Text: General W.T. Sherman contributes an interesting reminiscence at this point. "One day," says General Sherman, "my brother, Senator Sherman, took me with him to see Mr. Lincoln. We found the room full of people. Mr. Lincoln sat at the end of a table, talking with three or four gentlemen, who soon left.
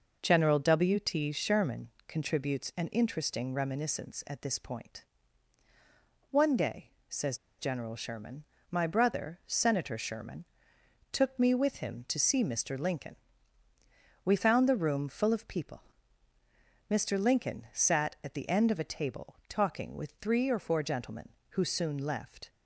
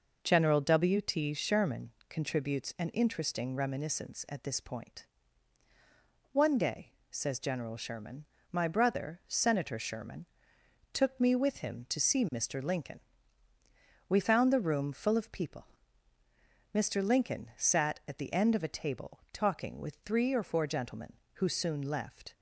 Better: second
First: pauses between "Sherman" and "contributes"; slight; at 1.8 s; 0.20 s long // pauses between "says" and "General"; slight; at 7.3 s; 0.22 s long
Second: pauses between "Sherman" and "contributes"; slight; at 1.9 s; 0.20 s long

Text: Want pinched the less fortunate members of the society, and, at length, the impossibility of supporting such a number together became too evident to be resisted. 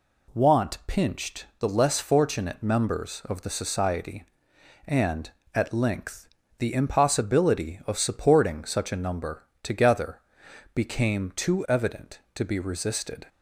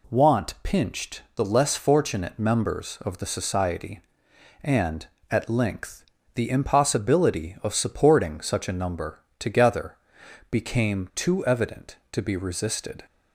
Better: neither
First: pauses between "number" and "together"; slight; at 9.4 s; 0.18 s long // pauses between "together" and "became"; noticeable; at 10.1 s; 0.56 s long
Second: pauses between "number" and "together"; slight; at 9.2 s; 0.18 s long // pauses between "together" and "became"; noticeable; at 9.9 s; 0.56 s long

